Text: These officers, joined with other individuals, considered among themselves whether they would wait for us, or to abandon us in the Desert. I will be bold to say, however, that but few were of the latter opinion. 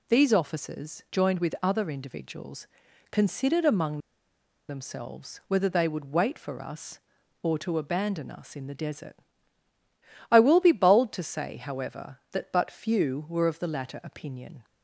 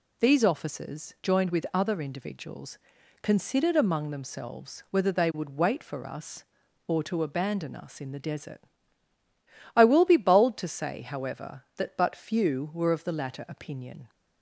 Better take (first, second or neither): second